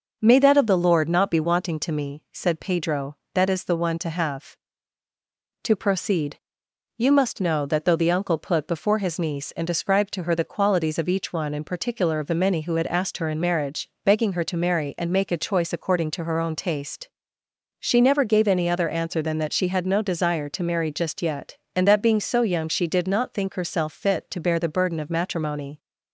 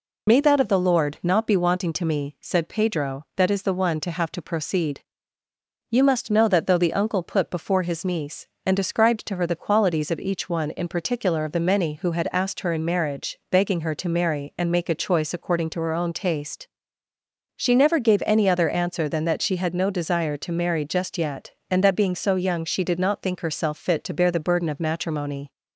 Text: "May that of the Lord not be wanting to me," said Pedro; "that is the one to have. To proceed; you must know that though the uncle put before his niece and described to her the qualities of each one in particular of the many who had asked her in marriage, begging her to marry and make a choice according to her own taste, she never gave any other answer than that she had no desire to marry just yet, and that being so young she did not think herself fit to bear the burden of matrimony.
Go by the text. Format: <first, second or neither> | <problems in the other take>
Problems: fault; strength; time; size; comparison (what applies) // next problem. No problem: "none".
first | loses the start of "May"; at 0.2 s; 40 ms